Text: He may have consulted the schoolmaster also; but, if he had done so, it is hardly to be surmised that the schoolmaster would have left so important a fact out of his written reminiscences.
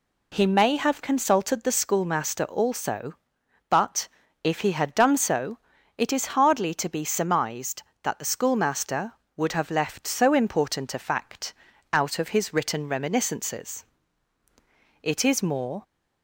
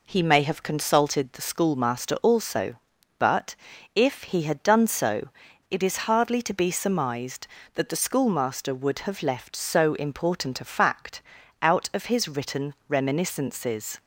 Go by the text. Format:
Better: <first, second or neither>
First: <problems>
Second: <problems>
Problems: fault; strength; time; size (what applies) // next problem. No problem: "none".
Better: second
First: pauses between "fact" and "out"; at 11.5 s; 0.38 s long // goes on to say "It is more"; noticeable; from 15.0 s on; 0.80 s long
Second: pauses between "fact" and "out"; at 11.1 s; 0.42 s long